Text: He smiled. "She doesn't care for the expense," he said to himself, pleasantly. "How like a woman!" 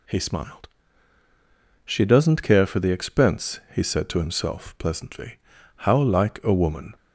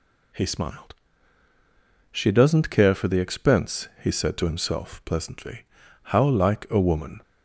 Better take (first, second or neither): neither